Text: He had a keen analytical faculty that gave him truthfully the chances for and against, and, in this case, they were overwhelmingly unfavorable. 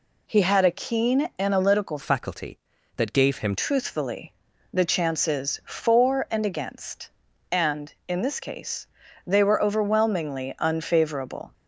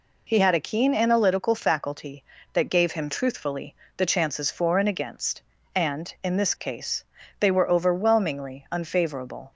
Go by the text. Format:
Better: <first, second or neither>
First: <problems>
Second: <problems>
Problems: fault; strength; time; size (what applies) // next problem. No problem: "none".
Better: second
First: changes voice from "faculty" to "him"; from 2.0 to 3.5 s; 1.5 s long // pauses between "truthfully" and "the"; at 4.3 s; 0.40 s long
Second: pauses between "truthfully" and "the"; slight; at 3.7 s; 0.22 s long